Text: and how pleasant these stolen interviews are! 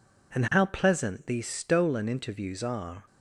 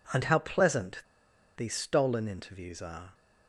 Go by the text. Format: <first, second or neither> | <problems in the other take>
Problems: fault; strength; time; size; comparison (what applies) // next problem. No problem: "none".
first | pauses between "pleasant" and "these"; noticeable; at 1.0 s; 0.56 s long